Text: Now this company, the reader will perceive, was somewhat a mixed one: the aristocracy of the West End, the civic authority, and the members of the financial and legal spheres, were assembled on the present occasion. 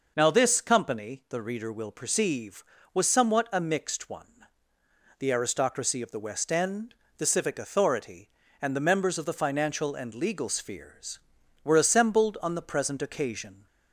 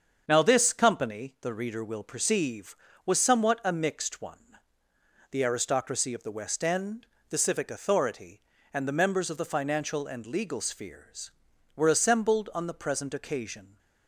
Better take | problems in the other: first | gets quieter; noticeable; throughout; 5 dB

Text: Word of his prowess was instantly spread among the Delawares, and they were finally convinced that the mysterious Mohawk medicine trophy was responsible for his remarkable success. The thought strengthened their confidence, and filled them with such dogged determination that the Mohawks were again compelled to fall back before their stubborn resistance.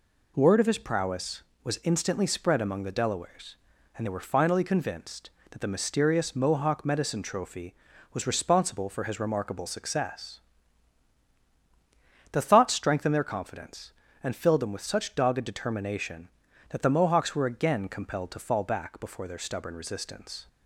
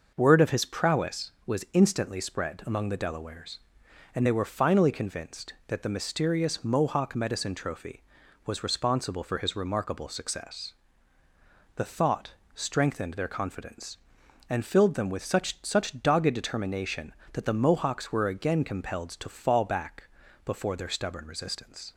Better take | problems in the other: first | pauses between "thought" and "strengthened"; slight; at 12.3 s; 0.22 s long // says "such" twice; at 15.6 s // pauses between "back" and "before"; slight; at 20.0 s; 0.36 s long

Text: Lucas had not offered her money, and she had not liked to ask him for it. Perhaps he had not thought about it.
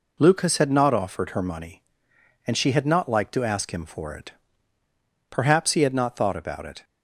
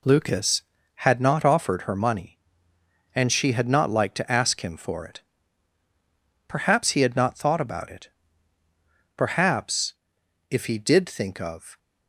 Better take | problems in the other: first | goes on to say "Perhaps if he did think of"; strong; from 9.1 s on; 2.6 s long

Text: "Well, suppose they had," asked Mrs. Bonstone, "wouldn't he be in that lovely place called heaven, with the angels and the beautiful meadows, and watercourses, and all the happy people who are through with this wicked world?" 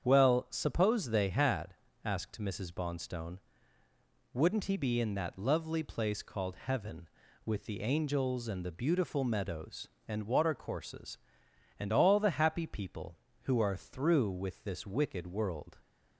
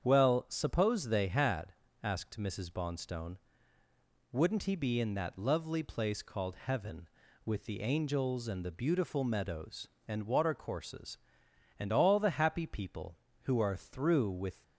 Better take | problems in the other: first | starts louder than the rest; strong; until 1.0 s; 8 dB; strong in the first // stops before "this wicked world"; at 14.6 s

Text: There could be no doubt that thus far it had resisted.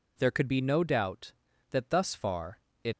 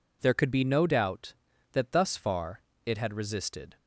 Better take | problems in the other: second | pauses between "far" and "it"; slight; at 2.6 s; 0.24 s long; slight in the second // stops before "had resisted"; at 2.9 s

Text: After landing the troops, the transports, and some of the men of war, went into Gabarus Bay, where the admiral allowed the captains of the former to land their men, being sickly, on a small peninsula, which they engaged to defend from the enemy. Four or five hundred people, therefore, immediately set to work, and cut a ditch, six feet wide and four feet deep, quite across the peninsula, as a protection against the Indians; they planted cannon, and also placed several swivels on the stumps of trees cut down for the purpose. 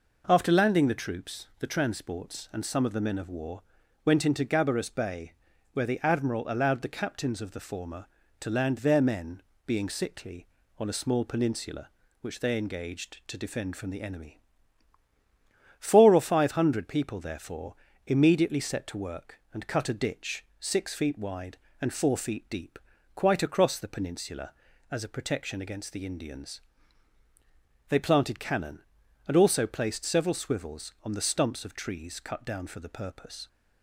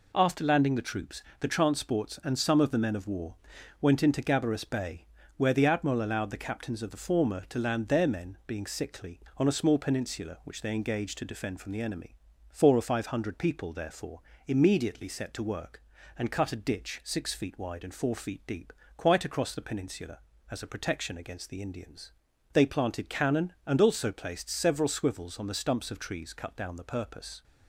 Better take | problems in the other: first | skips "for"; at 26.7 s

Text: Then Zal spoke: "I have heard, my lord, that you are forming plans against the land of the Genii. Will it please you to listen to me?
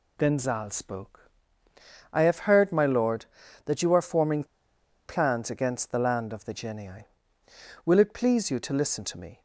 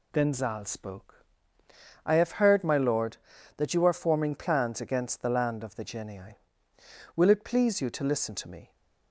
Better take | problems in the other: second | pauses between "forming" and "plans"; noticeable; at 4.4 s; 0.64 s long

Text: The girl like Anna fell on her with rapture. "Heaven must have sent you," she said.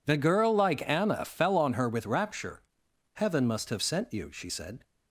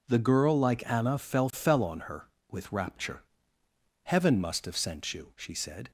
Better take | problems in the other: first | says "fell" twice; at 1.5 s

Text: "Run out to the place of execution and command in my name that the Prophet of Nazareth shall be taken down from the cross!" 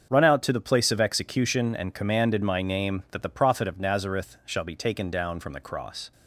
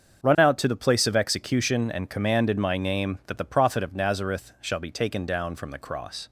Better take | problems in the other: neither | starts louder than the rest; the same in both

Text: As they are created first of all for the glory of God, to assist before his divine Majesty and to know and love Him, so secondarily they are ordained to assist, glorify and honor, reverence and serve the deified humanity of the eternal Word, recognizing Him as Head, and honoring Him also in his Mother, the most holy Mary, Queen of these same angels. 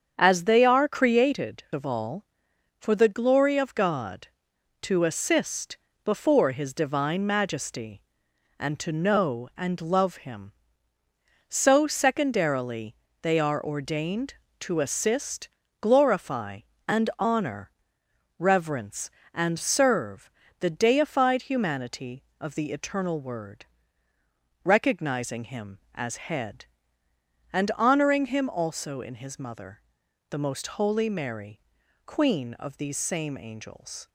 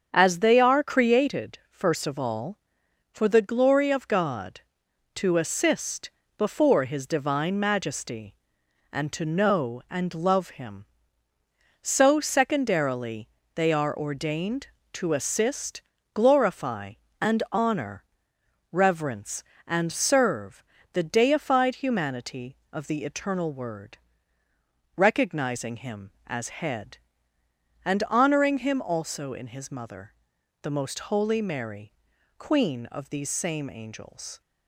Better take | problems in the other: second | starts louder than the rest; strong; until 1.1 s; 7.5 dB; strong in the second // skips "first"; at 1.6 s // pauses between "assist" and "before"; slight; at 5.7 s; 0.28 s long; slight in the second // pauses between "secondarily" and "they"; slight; at 12.9 s; 0.28 s long; slight in the second // pauses between "serve" and "the"; slight; at 20.3 s; 0.30 s long; slight in the second

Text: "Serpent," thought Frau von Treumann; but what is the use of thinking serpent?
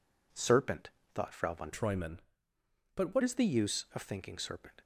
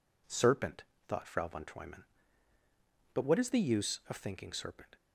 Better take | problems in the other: second | changes voice from "Treumann" to "what"; from 1.7 to 3.2 s; 1.5 s long

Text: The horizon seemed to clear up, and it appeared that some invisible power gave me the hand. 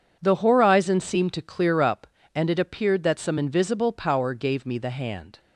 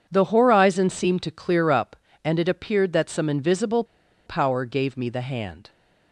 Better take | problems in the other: first | pauses between "invisible" and "power"; at 3.8 s; 0.42 s long

